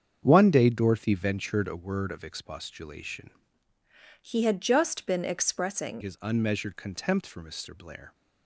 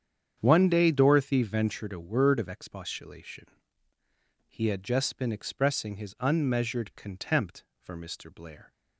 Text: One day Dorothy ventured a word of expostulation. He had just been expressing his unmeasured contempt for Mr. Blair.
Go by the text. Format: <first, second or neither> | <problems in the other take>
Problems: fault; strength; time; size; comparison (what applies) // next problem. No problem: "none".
second | starts louder than the rest; strong; until 1.2 s; 7.5 dB; strong in the second // changes voice from "He" to "expressing"; from 4.2 to 6.0 s; 1.8 s long